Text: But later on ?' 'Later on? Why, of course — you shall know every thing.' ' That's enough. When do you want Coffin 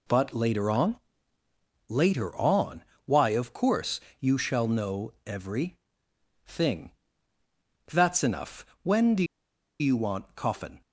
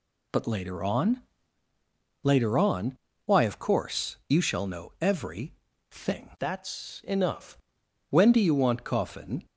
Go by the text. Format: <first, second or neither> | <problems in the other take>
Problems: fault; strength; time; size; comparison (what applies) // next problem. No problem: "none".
second | pauses between "every" and "thing"; noticeable; at 5.7 s; 0.70 s long; slight in the second // pauses between "do" and "you"; noticeable; at 9.2 s; 0.56 s long